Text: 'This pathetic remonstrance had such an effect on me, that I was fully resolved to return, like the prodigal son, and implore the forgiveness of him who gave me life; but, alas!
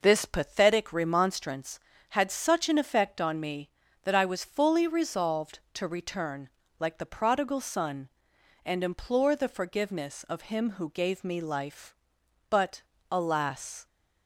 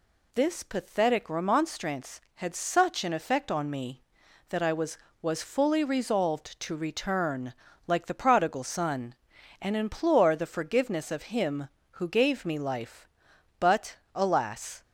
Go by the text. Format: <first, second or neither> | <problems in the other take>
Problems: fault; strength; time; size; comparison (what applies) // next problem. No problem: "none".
first | says "was" twice; at 5.2 s